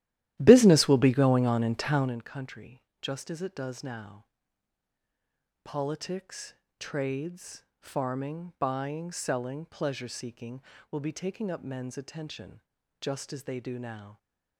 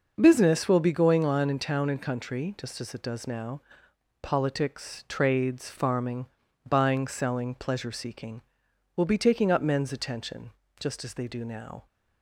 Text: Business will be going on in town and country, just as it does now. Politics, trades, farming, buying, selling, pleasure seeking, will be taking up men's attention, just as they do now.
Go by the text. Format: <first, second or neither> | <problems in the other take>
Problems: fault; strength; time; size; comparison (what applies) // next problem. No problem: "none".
second | starts louder than the rest; strong; until 2.3 s; 13.5 dB